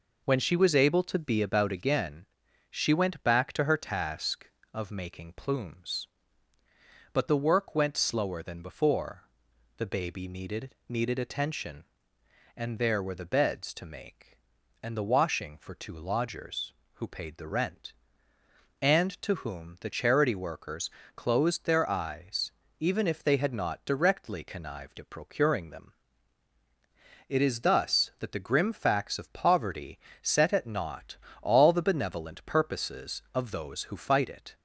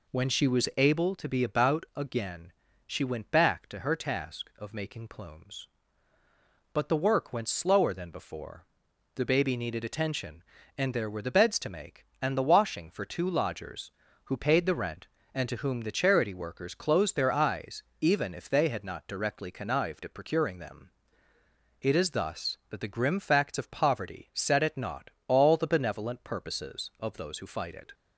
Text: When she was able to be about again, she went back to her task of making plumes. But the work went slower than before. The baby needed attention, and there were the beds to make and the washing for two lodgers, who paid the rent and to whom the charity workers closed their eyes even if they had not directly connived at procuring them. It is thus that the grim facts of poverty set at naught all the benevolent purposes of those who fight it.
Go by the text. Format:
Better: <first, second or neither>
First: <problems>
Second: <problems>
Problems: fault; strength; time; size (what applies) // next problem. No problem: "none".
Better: second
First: says "needed" twice; at 10.8 s // pauses between "workers" and "closed"; slight; at 20.8 s; 0.26 s long // pauses between "eyes" and "even"; slight; at 22.5 s; 0.28 s long // pauses between "poverty" and "set"; slight; at 29.9 s; 0.22 s long // pauses between "naught" and "all"; slight; at 31.1 s; 0.24 s long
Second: pauses between "eyes" and "even"; slight; at 17.8 s; 0.18 s long // pauses between "naught" and "all"; slight; at 25.0 s; 0.18 s long